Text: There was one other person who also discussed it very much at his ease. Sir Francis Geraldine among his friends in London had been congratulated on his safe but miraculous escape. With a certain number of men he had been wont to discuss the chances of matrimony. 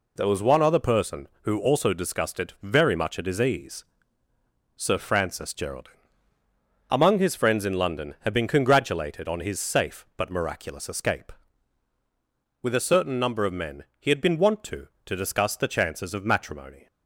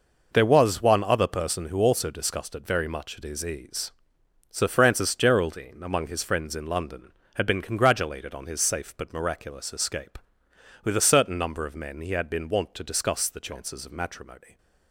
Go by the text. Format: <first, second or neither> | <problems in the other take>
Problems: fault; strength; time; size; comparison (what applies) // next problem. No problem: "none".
second | pauses between "Geraldine" and "among"; noticeable; at 5.9 s; 0.96 s long // pauses between "men" and "he"; slight; at 13.8 s; 0.16 s long // says "to" twice; at 15.0 s